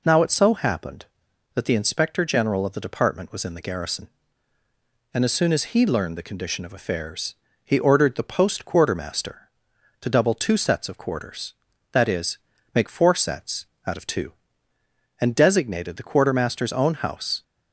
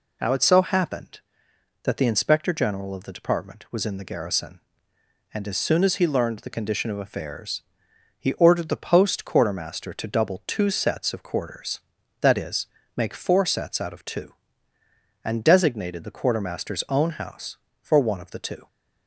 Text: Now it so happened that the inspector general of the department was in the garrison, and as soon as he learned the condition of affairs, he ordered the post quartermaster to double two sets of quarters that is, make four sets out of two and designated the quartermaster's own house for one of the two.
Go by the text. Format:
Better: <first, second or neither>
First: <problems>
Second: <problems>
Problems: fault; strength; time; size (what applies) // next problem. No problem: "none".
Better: second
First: pauses between "sets" and "out"; slight; at 13.6 s; 0.20 s long // stops before "for one of the two"; at 17.4 s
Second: none